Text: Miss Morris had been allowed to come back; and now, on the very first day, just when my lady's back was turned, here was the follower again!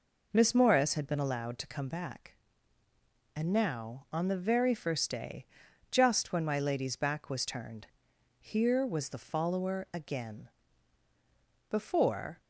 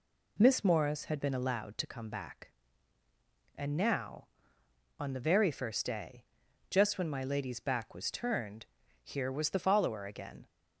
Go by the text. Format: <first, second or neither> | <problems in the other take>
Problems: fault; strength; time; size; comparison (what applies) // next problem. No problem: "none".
second | goes on to say "Before"; noticeable; from 11.6 s on; 0.72 s long